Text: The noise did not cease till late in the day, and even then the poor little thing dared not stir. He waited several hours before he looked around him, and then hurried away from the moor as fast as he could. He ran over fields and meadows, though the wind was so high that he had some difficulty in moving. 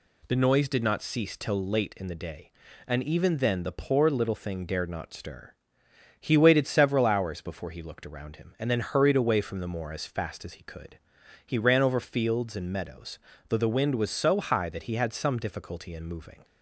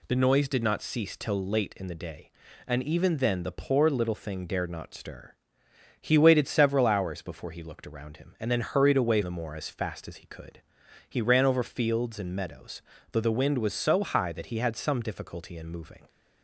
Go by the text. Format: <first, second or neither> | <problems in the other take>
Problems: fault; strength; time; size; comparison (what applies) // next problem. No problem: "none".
first | skips "from"; at 9.2 s